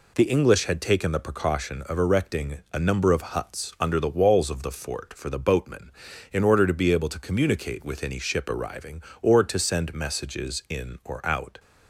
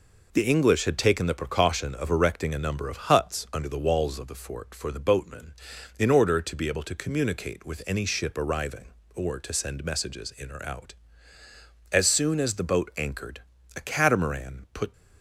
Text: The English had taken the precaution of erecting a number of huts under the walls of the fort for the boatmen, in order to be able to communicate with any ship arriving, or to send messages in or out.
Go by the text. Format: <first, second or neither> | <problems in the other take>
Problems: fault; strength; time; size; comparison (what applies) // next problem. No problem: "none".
first | goes on to say "As soon as the boat anchored a catamaran put"; strong; from 11.9 s on; 3.0 s long